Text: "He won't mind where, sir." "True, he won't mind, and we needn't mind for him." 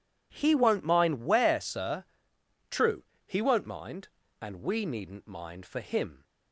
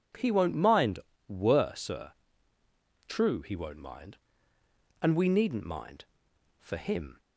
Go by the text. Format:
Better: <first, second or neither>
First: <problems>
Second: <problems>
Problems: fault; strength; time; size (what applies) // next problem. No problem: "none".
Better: first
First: none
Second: says "were" for "where"; at 1.2 s